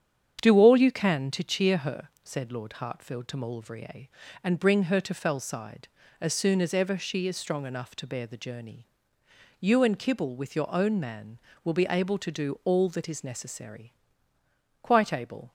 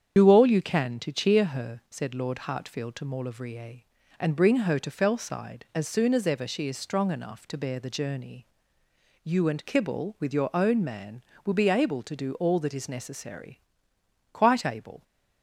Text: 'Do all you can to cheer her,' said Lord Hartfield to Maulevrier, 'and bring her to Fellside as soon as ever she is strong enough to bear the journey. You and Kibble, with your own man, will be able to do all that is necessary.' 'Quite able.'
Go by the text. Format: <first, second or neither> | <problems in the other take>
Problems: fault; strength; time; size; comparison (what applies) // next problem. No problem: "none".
first | loses the start of "Do"; at 0.1 s; 35 ms // starts louder than the rest; strong; until 1.1 s; 8 dB; strong in the first